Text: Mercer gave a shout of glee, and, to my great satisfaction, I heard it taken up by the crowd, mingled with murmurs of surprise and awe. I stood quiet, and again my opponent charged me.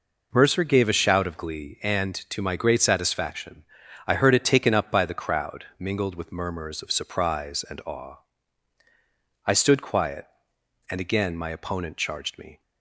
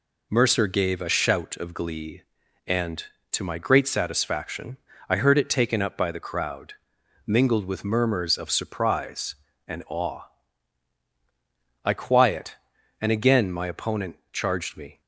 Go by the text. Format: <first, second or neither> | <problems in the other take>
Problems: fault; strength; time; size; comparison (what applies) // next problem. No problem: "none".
first | skips "stood"; at 11.9 s // pauses between "opponent" and "charged"; slight; at 14.1 s; 0.16 s long